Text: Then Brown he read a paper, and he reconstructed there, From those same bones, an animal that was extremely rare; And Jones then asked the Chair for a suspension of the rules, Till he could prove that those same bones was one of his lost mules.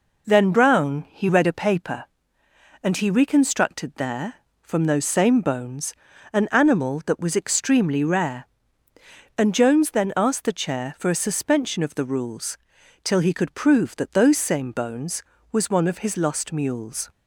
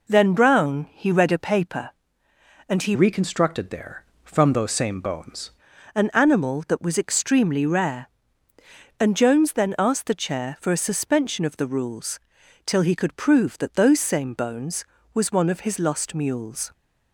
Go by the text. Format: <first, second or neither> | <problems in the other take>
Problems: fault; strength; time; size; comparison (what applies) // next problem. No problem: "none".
first | changes voice from "reconstructed" to "bones"; from 2.9 to 5.4 s; 2.5 s long